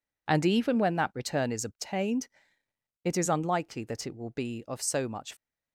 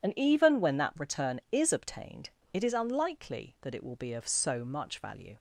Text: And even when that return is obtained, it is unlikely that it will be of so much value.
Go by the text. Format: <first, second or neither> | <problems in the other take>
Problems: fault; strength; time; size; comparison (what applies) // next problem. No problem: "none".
second | stops before "value"; at 5.3 s